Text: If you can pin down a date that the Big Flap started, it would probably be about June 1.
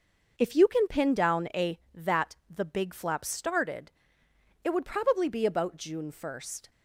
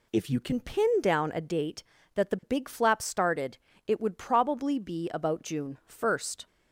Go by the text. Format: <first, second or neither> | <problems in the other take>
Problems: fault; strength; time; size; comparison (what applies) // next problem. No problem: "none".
second | skips "date"; at 1.8 s